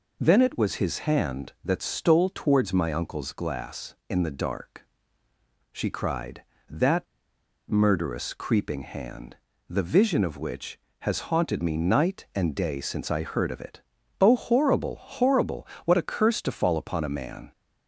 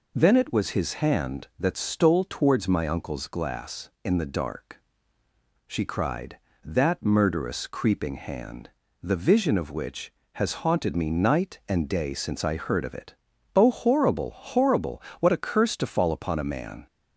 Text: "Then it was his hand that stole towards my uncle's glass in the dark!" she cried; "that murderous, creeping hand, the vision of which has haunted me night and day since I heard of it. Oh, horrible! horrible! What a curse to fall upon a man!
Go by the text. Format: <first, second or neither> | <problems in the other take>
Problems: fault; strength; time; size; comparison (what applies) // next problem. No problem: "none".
second | pauses between "that" and "murderous"; noticeable; at 7.0 s; 0.64 s long